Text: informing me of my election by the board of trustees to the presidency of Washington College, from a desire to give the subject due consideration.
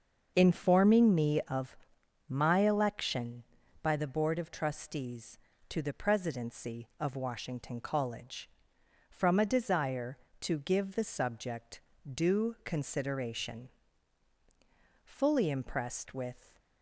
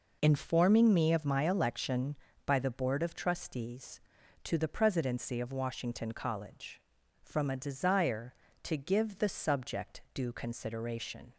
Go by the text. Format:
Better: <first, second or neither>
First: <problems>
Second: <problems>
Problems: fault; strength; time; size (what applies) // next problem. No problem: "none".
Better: second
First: starts louder than the rest; until 1.3 s; 6.5 dB // pauses between "of" and "my"; noticeable; at 1.7 s; 0.52 s long // pauses between "subject" and "due"; slight; at 11.8 s; 0.32 s long // goes on to say "Fully impressed with"; from 15.0 s on; 1.5 s long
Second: none